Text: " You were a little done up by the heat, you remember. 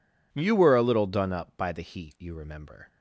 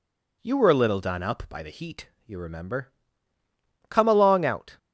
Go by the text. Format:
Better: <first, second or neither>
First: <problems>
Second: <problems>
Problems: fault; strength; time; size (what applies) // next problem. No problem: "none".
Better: first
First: none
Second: goes on to say "Come along out"; noticeable; from 3.8 s on; 0.88 s long